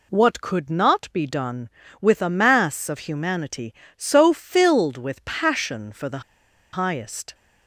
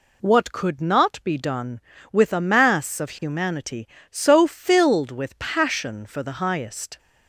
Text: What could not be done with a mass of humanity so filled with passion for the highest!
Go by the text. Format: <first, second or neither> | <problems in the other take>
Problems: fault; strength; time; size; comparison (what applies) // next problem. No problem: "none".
second | pauses between "the" and "highest"; noticeable; at 6.2 s; 0.53 s long